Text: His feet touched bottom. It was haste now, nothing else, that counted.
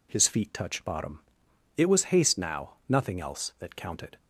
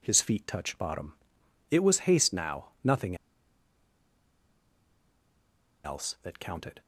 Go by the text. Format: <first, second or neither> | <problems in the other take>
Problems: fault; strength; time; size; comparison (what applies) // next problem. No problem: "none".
first | pauses between "nothing" and "else"; strong; at 3.1 s; 2.6 s long